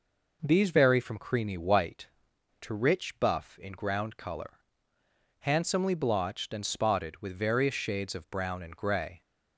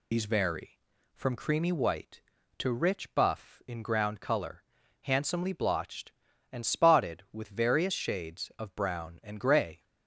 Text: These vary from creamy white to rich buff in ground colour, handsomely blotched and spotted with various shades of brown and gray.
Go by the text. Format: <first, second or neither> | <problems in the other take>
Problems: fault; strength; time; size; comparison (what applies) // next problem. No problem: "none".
first | loses the start of "These"; at 0.1 s; 80 ms